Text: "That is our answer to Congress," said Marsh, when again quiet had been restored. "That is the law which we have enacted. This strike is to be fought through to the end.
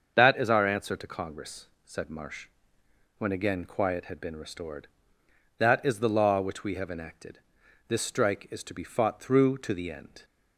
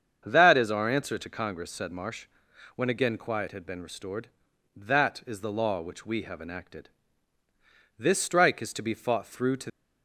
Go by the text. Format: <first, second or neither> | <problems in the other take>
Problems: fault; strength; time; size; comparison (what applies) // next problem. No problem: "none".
first | starts louder than the rest; strong; until 1.2 s; 7.5 dB; also in the first // stops before "the end"; at 9.6 s